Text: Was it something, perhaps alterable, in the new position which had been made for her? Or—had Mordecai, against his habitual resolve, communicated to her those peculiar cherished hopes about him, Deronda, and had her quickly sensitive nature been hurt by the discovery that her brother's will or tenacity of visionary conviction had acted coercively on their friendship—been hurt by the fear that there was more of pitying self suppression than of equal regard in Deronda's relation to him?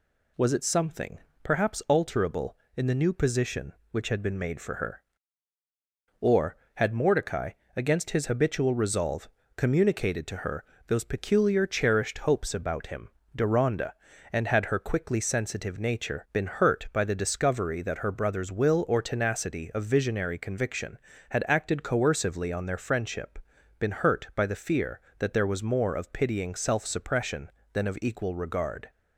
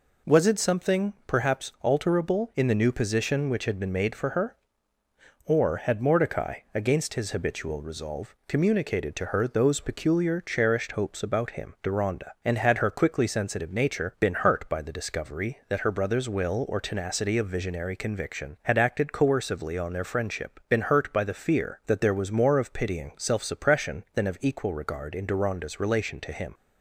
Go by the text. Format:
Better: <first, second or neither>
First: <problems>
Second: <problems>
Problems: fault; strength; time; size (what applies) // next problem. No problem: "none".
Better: second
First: pauses between "her" and "those"; slight; at 10.6 s; 0.24 s long // stops before "in Deronda's relation to him"; at 28.8 s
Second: none